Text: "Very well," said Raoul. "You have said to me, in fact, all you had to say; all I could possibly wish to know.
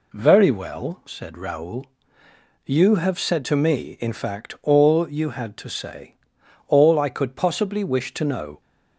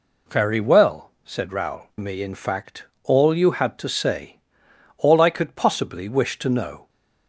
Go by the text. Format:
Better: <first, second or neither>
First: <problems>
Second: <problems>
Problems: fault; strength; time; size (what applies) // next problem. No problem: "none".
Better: first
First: none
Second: skips "You have said to"; at 1.9 s